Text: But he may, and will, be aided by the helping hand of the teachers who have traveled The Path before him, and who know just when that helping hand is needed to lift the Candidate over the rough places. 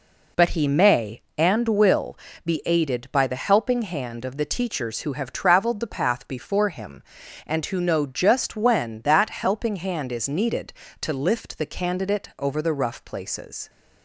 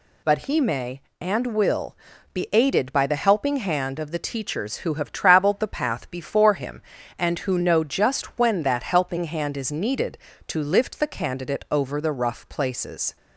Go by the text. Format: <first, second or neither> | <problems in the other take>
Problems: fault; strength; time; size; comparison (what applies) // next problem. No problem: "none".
neither | none